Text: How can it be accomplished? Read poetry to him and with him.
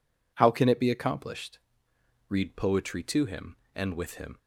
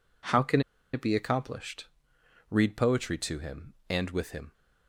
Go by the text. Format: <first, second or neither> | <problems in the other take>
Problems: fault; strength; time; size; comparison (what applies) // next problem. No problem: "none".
first | pauses between "can" and "it"; slight; at 0.6 s; 0.31 s long